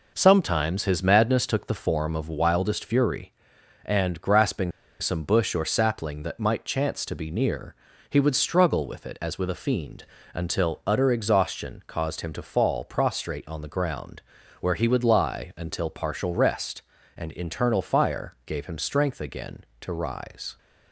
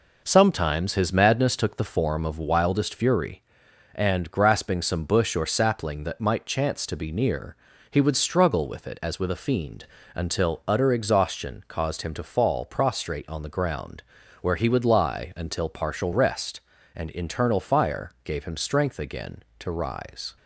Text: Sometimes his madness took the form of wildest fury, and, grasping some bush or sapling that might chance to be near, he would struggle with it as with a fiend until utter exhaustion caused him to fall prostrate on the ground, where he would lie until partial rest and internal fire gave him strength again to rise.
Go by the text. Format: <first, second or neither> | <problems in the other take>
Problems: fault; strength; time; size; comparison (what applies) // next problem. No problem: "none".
second | pauses between "grasping" and "some"; slight; at 4.7 s; 0.29 s long // pauses between "fiend" and "until"; slight; at 10.0 s; 0.30 s long; slight in the second